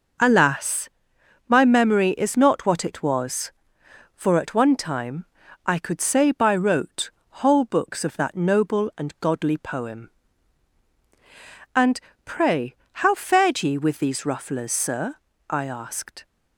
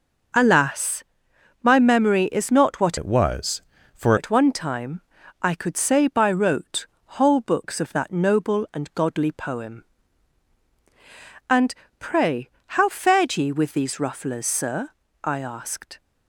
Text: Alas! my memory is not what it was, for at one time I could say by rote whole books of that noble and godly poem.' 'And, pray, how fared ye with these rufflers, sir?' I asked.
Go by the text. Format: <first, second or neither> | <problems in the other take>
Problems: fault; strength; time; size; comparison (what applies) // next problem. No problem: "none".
first | changes voice from "it" to "for"; from 2.9 to 4.1 s; 1.2 s long // pauses between "time" and "I"; at 4.9 s; 0.40 s long; also in the first // pauses between "rote" and "whole"; slight; at 6.8 s; 0.32 s long; slight in the first